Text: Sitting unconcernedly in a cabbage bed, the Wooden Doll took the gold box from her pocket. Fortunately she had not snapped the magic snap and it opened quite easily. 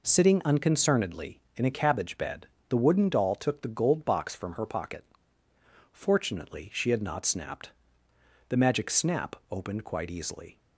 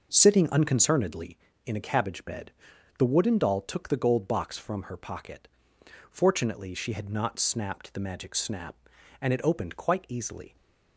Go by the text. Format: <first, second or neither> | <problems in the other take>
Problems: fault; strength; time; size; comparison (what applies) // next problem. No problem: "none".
second | pauses between "snapped" and "the"; noticeable; at 7.7 s; 0.78 s long // skips "and it"; at 9.4 s